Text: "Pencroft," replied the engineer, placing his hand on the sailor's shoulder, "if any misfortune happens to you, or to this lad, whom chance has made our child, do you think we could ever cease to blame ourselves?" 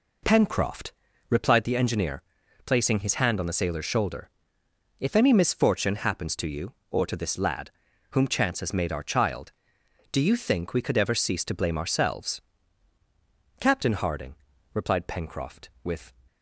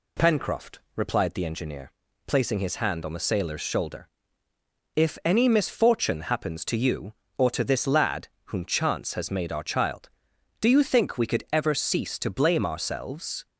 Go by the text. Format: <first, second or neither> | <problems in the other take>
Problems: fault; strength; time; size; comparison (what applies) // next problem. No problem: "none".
second | goes on to say "Captain Harding replied Pencroft with"; strong; from 13.5 s on; 2.5 s long